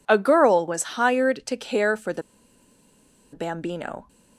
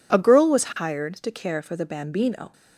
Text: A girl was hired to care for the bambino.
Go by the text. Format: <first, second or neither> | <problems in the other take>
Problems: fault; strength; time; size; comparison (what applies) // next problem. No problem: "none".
second | pauses between "the" and "bambino"; at 2.2 s; 1.1 s long